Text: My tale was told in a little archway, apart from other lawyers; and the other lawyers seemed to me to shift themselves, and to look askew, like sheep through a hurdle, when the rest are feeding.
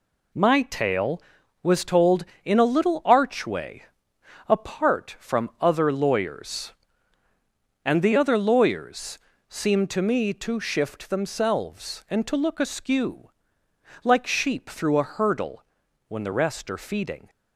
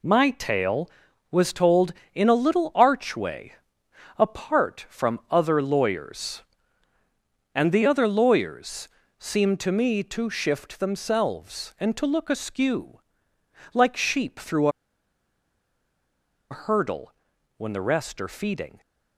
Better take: first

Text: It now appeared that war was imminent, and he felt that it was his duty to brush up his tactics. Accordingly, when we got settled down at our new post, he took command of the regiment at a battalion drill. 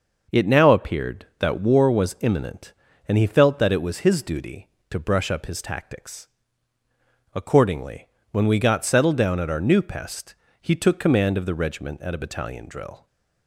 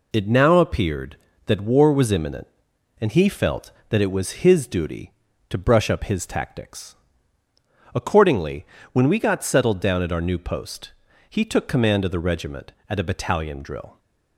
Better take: second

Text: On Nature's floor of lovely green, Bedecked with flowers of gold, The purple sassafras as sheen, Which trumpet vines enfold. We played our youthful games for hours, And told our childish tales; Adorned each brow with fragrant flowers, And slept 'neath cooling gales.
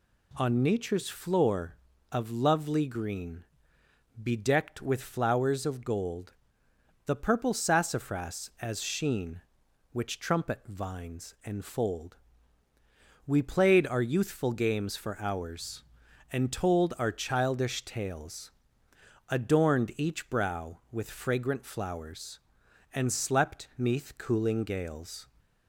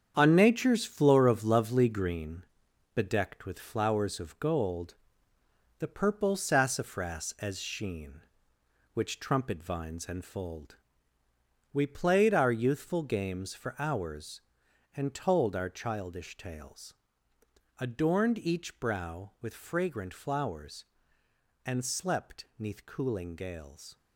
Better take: first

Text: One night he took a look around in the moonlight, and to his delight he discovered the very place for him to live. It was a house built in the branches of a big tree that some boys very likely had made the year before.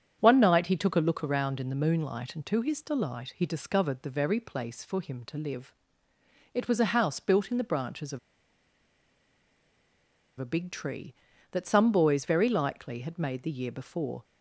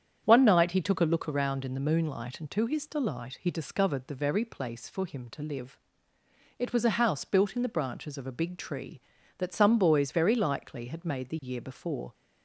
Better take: second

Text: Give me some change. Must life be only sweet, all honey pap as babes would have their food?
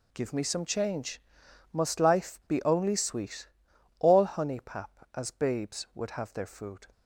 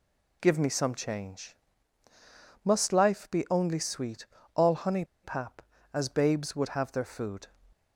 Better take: first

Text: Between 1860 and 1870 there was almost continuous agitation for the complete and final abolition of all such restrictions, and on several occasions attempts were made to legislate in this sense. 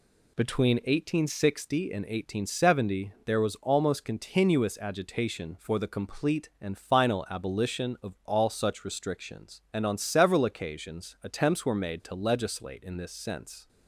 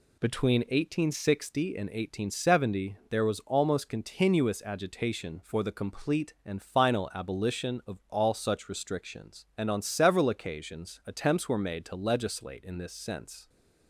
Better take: neither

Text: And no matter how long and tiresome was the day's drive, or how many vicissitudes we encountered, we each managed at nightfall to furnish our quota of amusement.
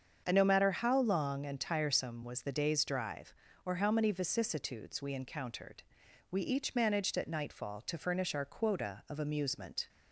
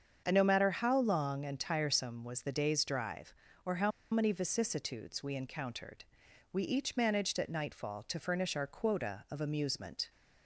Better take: first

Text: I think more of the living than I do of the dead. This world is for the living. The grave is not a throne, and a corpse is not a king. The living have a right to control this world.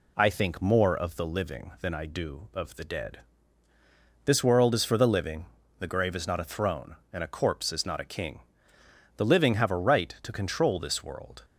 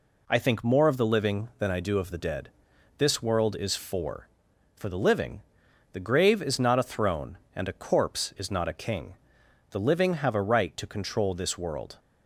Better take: first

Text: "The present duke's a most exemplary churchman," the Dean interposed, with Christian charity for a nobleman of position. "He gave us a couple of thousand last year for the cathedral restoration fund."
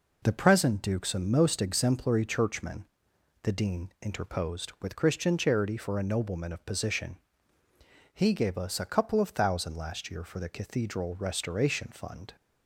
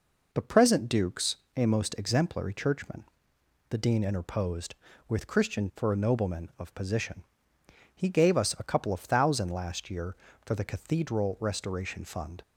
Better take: first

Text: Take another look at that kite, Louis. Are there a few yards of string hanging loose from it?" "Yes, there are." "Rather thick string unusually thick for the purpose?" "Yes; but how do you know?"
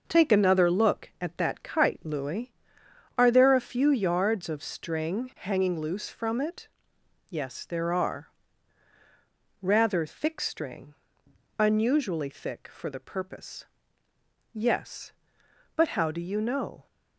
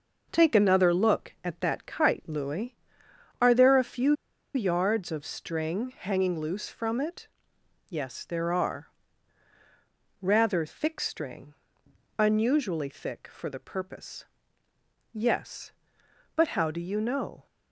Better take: first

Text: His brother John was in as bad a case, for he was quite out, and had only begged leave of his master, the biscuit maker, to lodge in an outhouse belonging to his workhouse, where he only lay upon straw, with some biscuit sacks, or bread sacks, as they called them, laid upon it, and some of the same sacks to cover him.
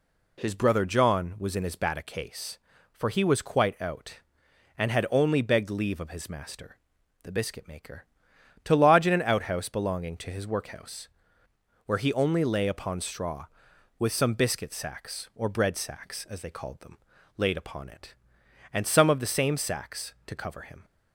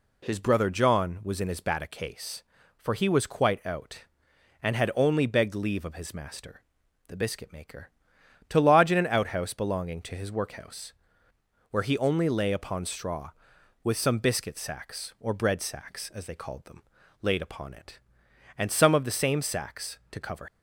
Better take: first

